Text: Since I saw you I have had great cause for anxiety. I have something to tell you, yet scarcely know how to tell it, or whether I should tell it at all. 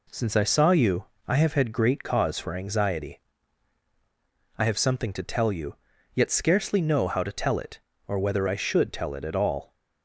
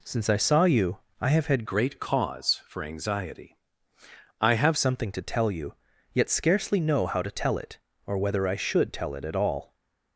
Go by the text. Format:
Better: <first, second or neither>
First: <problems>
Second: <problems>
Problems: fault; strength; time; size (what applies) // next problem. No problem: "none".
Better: first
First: pauses between "you" and "I"; slight; at 1.0 s; 0.22 s long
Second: pauses between "you" and "I"; slight; at 0.9 s; 0.22 s long // changes voice from "great" to "have"; from 1.6 to 4.7 s; 3.1 s long